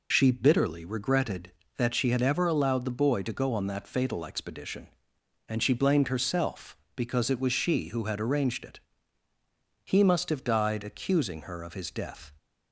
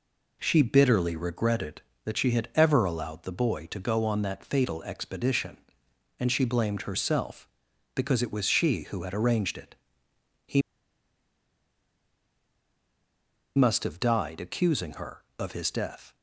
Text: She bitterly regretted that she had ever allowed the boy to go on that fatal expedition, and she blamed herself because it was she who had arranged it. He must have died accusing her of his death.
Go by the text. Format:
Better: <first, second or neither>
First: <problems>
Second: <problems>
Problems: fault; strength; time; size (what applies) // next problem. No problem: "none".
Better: first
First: none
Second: pauses between "He" and "must"; strong; at 10.6 s; 2.9 s long